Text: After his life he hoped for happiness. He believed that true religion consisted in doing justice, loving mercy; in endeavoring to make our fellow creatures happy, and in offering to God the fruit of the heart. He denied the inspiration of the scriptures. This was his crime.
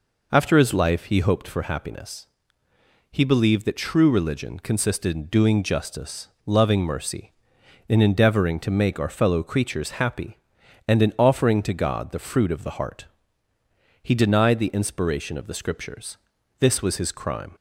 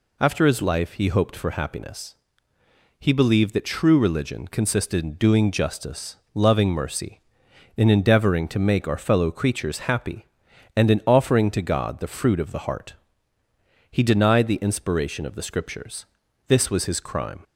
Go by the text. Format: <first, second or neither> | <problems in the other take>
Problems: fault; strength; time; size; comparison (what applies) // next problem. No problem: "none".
second | starts louder than the rest; noticeable; until 1.3 s; 4.5 dB